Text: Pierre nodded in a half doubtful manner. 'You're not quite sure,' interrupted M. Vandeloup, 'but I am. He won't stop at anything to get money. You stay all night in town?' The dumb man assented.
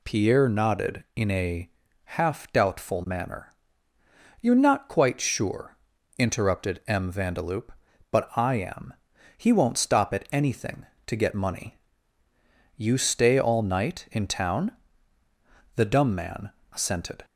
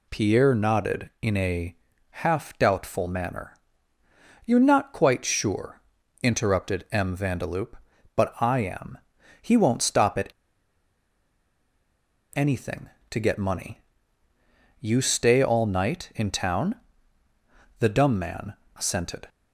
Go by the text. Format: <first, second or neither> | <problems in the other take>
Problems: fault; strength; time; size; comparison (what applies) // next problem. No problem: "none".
first | pauses between "a" and "half"; slight; at 1.7 s; 0.34 s long; slight in the first // pauses between "at" and "anything"; strong; at 10.3 s; 2.0 s long // pauses between "man" and "assented"; slight; at 18.5 s; 0.22 s long; slight in the first